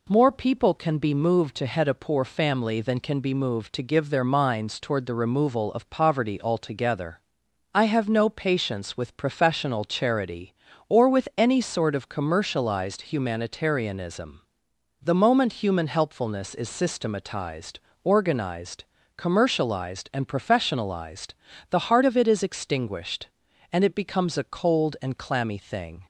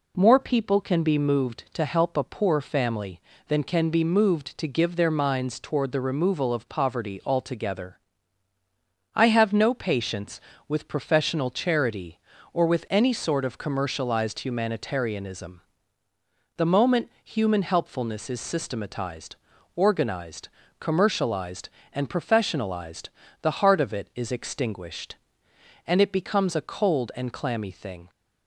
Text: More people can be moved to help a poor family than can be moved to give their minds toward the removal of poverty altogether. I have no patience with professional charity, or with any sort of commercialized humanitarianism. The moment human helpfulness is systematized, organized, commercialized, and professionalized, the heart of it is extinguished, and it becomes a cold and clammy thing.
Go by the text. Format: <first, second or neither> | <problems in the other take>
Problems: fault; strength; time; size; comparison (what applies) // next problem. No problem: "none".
second | says "head" for "help"; at 1.6 s